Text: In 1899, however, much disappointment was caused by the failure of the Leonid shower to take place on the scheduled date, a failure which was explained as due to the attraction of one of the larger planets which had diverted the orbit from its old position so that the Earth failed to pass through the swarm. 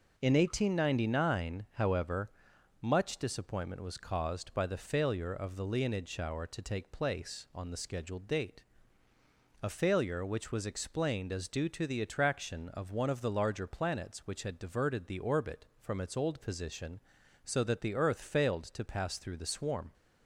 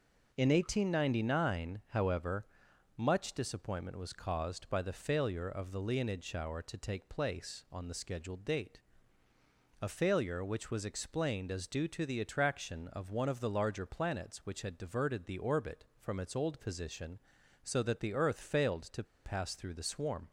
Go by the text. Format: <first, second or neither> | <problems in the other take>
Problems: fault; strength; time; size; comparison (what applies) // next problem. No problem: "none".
first | starts louder than the rest; noticeable; until 1.3 s; 6 dB // pauses between "to" and "pass"; slight; at 19.0 s; 0.20 s long